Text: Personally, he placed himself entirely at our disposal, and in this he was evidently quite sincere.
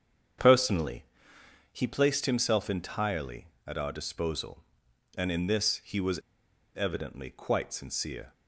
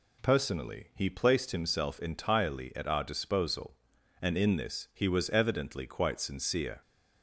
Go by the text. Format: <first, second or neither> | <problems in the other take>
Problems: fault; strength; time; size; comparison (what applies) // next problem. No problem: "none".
second | starts louder than the rest; strong; until 2.1 s; 8 dB // pauses between "was" and "evidently"; noticeable; at 6.1 s; 0.59 s long